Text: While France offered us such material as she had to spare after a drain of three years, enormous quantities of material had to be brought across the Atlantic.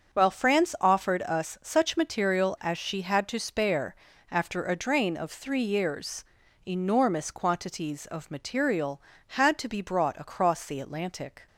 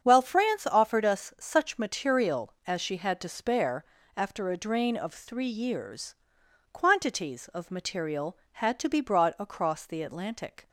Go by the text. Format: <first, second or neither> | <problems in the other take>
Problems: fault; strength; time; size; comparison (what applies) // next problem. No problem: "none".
first | starts louder than the rest; strong; until 1.0 s; 7.5 dB; also in the first // pauses between "spare" and "after"; slight; at 3.8 s; 0.32 s long; slight in the first // skips "enormous"; at 6.4 s